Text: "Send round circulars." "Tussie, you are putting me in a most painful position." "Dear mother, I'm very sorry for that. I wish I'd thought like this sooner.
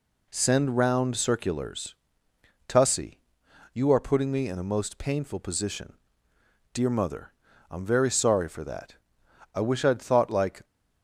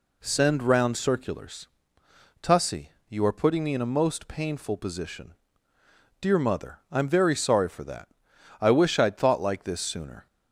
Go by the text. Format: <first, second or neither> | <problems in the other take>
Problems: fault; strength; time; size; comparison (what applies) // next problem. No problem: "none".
second | stops before "this sooner"; at 10.6 s